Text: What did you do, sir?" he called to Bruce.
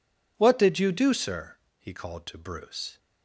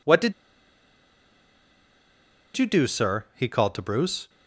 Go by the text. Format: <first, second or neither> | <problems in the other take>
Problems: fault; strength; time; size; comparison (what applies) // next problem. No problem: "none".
first | pauses between "did" and "you"; strong; at 0.3 s; 2.2 s long